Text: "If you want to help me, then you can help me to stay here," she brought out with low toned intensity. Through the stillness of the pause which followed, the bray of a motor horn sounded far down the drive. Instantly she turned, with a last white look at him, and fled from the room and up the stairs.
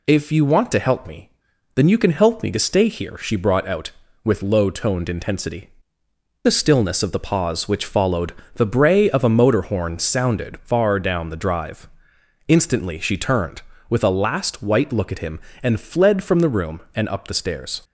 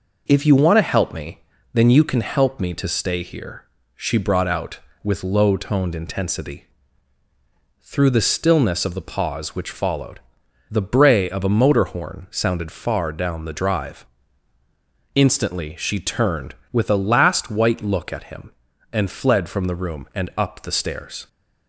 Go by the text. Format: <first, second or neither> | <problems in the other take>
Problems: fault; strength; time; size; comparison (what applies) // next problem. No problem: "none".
second | skips "Through"; at 6.0 s